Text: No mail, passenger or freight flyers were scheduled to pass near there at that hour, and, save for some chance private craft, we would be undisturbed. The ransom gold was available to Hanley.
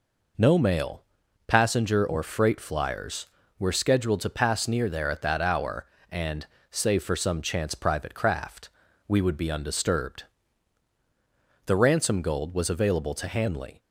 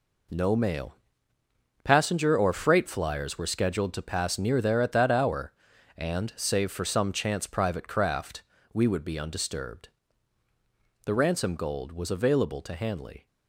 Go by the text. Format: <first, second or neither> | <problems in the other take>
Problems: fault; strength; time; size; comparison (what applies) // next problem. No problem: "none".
first | gets quieter; strong; throughout; 9 dB